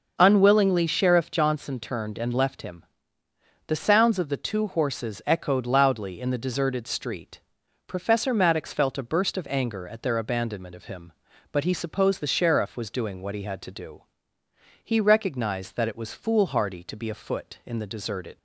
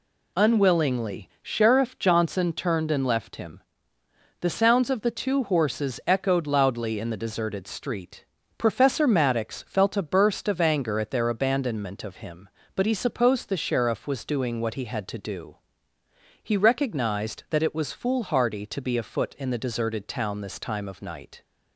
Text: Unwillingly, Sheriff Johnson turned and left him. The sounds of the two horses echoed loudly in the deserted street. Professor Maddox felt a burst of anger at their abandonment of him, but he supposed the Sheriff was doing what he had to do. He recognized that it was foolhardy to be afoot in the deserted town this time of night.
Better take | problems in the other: second | stops before "town this time of night"; at 18.3 s

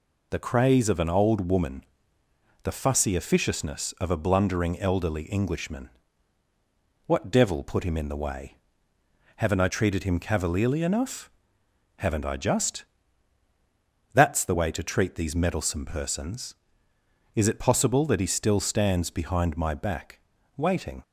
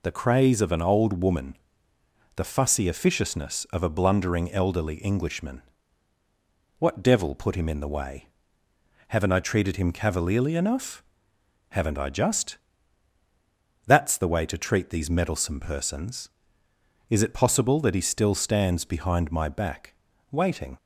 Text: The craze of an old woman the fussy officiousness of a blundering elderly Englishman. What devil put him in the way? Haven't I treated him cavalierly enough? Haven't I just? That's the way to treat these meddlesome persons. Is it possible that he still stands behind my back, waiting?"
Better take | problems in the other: neither | pauses between "woman" and "the"; noticeable; the same in both

